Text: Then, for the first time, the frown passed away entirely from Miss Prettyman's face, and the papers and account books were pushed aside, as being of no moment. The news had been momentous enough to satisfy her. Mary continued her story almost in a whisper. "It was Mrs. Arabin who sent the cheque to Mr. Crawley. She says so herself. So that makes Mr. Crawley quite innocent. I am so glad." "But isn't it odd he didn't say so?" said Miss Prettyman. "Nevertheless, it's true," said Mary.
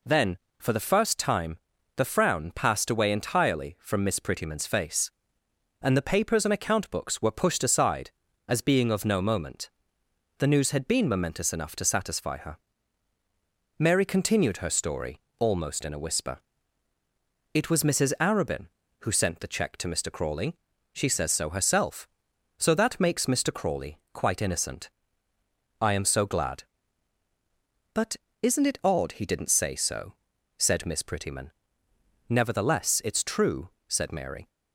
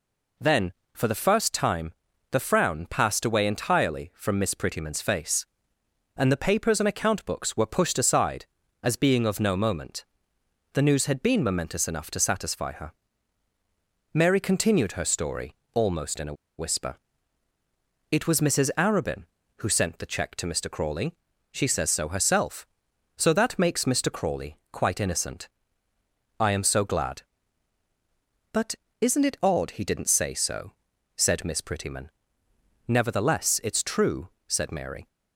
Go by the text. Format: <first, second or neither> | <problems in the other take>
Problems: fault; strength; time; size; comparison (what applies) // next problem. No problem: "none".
first | pauses between "story" and "almost"; slight; at 15.5 s; 0.18 s long; slight in the first // pauses between "a" and "whisper"; slight; at 16.3 s; 0.25 s long // pauses between "But" and "isn't"; slight; at 28.7 s; 0.26 s long; slight in the first